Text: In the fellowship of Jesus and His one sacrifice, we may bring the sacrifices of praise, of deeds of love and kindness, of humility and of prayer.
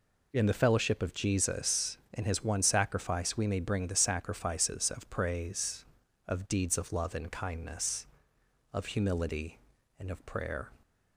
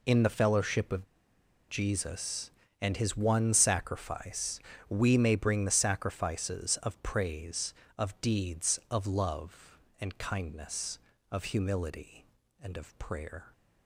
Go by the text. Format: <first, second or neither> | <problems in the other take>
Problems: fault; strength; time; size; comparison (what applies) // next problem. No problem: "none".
first | pauses between "of" and "Jesus"; noticeable; at 1.0 s; 0.63 s long